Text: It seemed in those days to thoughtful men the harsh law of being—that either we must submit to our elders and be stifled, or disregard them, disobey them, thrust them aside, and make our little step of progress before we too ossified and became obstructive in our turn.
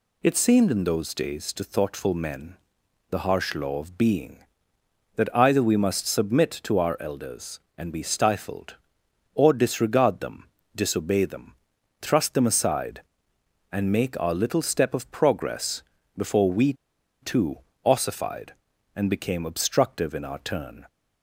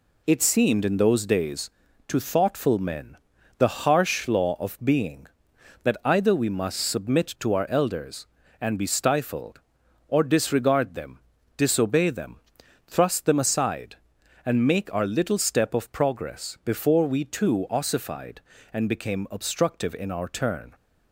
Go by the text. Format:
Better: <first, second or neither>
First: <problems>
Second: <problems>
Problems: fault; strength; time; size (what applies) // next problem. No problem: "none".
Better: second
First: pauses between "men" and "the"; noticeable; at 2.5 s; 0.56 s long // pauses between "progress" and "before"; slight; at 15.8 s; 0.32 s long // pauses between "we" and "too"; noticeable; at 16.7 s; 0.48 s long // pauses between "too" and "ossified"; slight; at 17.5 s; 0.28 s long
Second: pauses between "men" and "the"; at 3.1 s; 0.42 s long